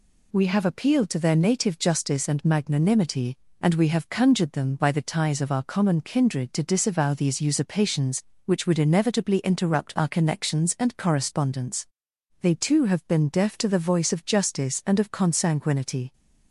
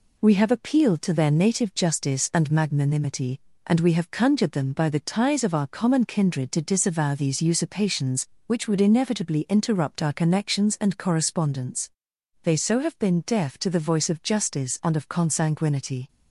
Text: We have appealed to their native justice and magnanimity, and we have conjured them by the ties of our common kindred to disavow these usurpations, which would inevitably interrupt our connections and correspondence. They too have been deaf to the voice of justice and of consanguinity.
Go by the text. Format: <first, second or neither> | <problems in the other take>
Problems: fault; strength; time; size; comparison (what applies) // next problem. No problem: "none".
first | says "so" for "too"; at 12.5 s